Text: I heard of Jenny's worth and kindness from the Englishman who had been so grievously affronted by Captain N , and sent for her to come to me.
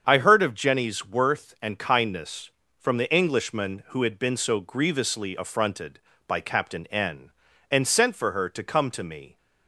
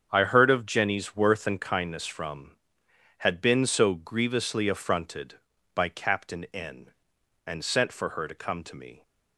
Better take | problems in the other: first | starts louder than the rest; strong; until 1.1 s; 7.5 dB; strong in the first // skips "the Englishman who"; at 2.8 s

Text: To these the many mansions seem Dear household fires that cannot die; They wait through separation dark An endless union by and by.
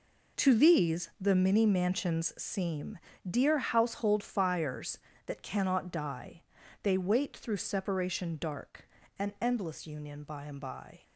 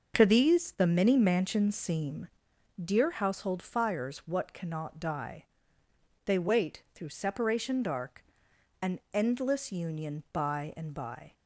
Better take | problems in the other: first | starts louder than the rest; until 1.2 s; 6.5 dB // pauses between "seem" and "Dear"; noticeable; at 2.2 s; 0.52 s long; slight in the first // says "what" for "that"; at 4.1 s // pauses between "dark" and "An"; noticeable; at 8.2 s; 0.58 s long; slight in the first

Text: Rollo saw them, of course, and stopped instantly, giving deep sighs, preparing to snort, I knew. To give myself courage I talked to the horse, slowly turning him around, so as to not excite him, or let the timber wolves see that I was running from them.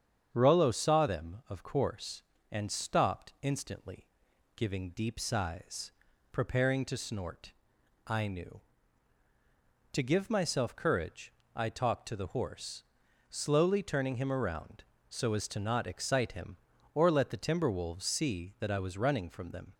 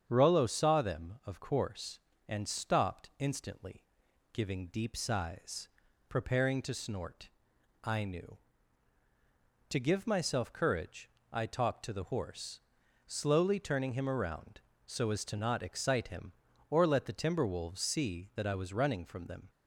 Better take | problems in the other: neither | starts louder than the rest; strong; the same in both // pauses between "courage" and "I"; slight; the same in both

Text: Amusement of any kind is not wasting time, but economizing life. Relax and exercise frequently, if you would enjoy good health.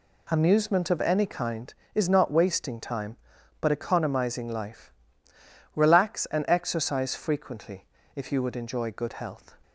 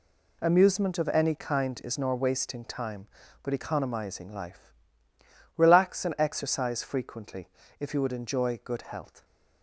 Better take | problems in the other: first | says "nor" for "not"; at 1.9 s

